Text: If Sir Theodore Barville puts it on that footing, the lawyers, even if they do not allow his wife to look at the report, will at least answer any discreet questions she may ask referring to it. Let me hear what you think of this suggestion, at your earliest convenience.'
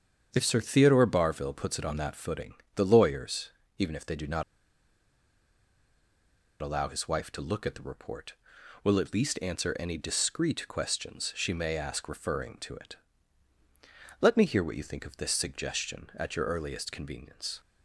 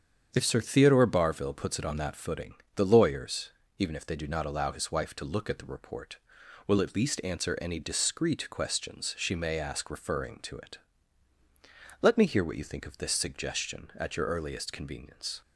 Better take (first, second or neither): second